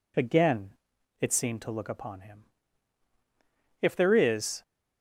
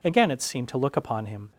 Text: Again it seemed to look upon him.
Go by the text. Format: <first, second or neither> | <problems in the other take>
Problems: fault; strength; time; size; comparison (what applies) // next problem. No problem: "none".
second | pauses between "Again" and "it"; noticeable; at 0.7 s; 0.46 s long // goes on to say "If there is"; noticeable; from 3.7 s on; 0.82 s long